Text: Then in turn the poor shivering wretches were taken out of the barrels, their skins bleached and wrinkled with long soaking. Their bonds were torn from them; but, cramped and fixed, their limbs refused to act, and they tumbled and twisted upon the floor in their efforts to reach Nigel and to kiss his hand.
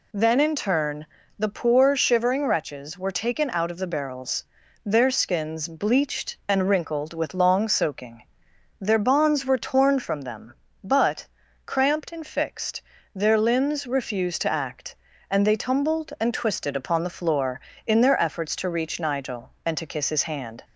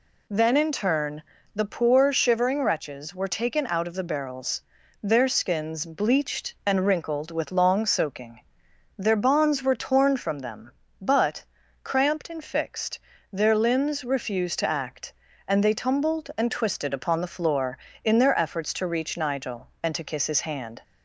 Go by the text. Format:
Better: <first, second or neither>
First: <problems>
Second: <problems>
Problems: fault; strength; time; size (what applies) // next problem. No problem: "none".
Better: neither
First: pauses between "turn" and "the"; slight; at 1.0 s; 0.32 s long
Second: pauses between "turn" and "the"; slight; at 1.2 s; 0.32 s long